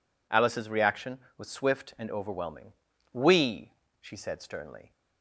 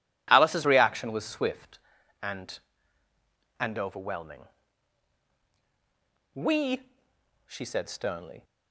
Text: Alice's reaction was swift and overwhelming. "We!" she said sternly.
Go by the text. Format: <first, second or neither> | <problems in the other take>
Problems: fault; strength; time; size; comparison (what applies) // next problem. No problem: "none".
first | says "and" twice; at 3.5 s